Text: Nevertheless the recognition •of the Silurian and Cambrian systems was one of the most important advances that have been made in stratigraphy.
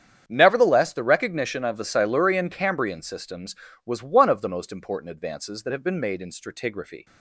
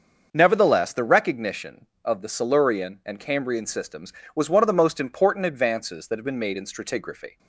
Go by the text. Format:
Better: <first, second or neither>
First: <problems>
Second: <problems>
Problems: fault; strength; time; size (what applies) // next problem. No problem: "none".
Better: second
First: starts louder than the rest; strong; until 1.2 s; 8 dB // skips "and"; at 2.4 s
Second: starts louder than the rest; until 1.3 s; 6.5 dB